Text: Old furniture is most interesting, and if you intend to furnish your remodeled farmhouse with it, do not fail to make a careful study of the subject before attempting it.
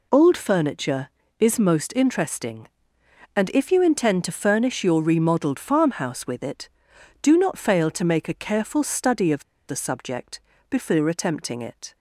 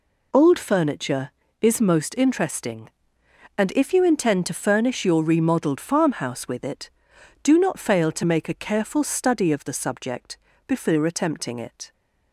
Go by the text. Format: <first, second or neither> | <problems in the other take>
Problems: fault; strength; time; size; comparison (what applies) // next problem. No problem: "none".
second | pauses between "of" and "the"; slight; at 9.4 s; 0.25 s long // pauses between "subject" and "before"; slight; at 10.3 s; 0.30 s long; slight in the second